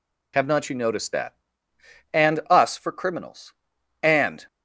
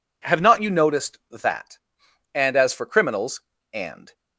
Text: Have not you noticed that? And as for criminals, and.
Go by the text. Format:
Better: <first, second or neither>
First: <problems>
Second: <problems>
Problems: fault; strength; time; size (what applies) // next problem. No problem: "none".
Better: second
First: says "us" for "as"; at 2.5 s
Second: none